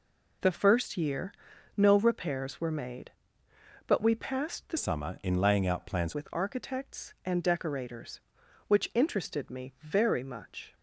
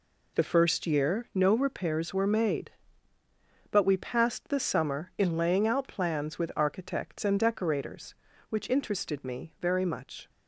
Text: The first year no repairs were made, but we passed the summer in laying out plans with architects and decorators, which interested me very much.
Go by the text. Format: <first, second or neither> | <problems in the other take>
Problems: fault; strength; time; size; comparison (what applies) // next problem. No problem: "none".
second | pauses between "year" and "no"; at 1.3 s; 0.42 s long // changes voice from "summer" to "plans"; from 4.7 to 6.1 s; 1.4 s long